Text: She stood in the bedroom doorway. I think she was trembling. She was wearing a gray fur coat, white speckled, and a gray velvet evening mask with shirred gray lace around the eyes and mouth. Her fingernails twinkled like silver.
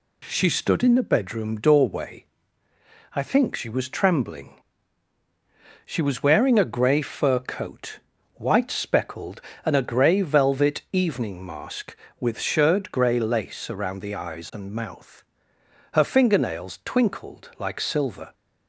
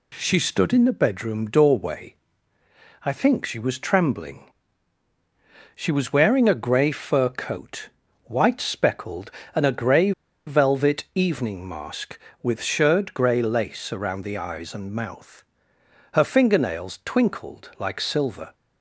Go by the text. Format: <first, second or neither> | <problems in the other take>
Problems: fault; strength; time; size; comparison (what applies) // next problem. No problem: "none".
first | pauses between "gray" and "velvet"; slight; at 10.1 s; 0.35 s long